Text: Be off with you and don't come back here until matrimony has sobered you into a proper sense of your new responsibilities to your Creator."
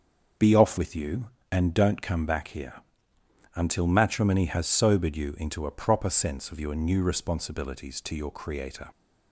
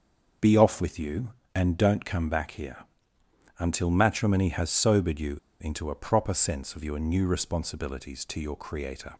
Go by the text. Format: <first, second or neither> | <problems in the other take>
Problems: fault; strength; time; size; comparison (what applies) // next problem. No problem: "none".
first | starts louder than the rest; until 1.6 s; 6.5 dB; also in the first // pauses between "here" and "until"; noticeable; at 2.7 s; 0.82 s long; noticeable in the first // pauses between "you" and "into"; slight; at 5.3 s; 0.24 s long